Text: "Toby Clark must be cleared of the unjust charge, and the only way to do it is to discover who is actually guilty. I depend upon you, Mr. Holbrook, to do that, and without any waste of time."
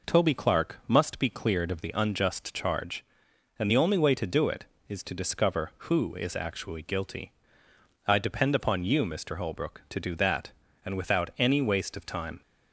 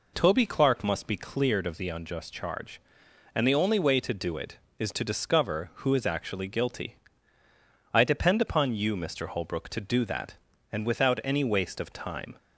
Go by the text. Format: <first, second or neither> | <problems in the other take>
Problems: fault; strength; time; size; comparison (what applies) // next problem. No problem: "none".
neither | none